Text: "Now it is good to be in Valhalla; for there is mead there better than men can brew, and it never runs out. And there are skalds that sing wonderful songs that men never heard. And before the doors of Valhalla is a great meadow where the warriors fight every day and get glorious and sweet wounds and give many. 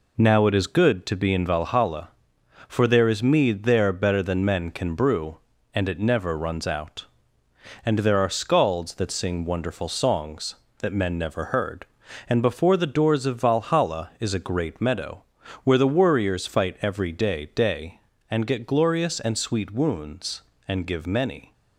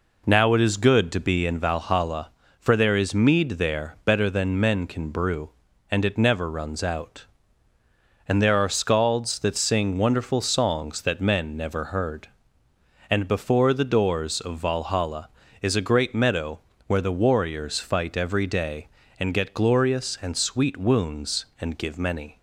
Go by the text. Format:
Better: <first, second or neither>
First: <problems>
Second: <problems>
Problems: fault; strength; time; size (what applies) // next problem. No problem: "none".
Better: second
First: pauses between "meadow" and "where"; at 15.2 s; 0.40 s long // says "day" twice; at 17.5 s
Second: pauses between "meadow" and "where"; slight; at 16.6 s; 0.26 s long